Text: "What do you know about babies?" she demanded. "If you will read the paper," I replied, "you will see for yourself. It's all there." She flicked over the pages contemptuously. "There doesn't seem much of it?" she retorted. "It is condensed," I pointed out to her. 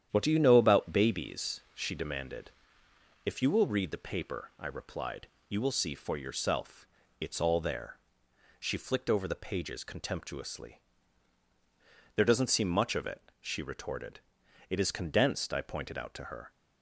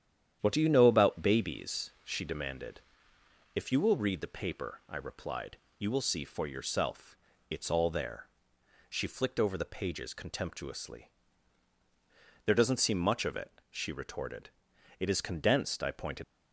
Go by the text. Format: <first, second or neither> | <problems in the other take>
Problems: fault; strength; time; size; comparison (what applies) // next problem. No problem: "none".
first | starts louder than the rest; strong; until 1.4 s; 9.5 dB; strong in the first // stops before "out to her"; at 16.2 s